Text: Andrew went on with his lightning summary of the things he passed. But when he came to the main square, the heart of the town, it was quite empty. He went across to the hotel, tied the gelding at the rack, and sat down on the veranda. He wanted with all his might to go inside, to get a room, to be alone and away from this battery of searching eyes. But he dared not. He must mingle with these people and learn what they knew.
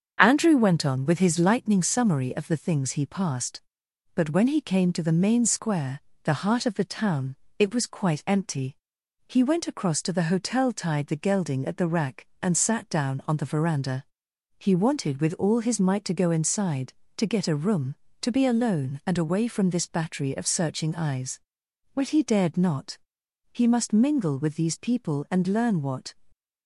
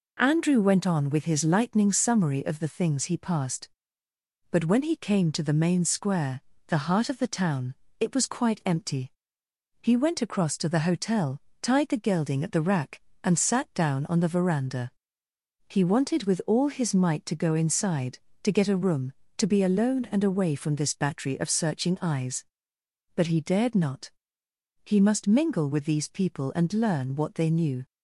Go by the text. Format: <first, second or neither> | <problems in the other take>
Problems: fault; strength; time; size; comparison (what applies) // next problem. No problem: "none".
second | starts louder than the rest; until 1.2 s; 6.5 dB // stops before "they knew"; at 26.3 s